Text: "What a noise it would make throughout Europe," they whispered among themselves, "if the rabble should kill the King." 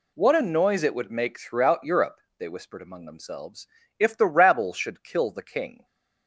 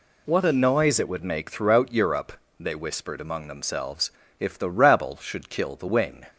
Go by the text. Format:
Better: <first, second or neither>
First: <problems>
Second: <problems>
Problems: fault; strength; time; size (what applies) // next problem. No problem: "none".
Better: first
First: none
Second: says "Wing" for "King"; at 5.8 s